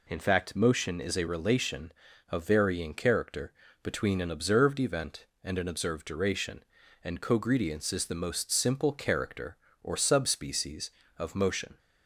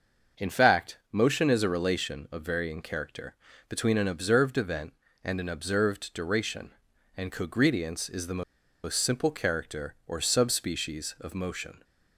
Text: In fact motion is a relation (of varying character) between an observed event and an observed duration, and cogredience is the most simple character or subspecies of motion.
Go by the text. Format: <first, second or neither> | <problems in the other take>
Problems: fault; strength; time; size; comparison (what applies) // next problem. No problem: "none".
first | starts louder than the rest; until 1.5 s; 6.5 dB // pauses between "the" and "most"; at 8.4 s; 0.42 s long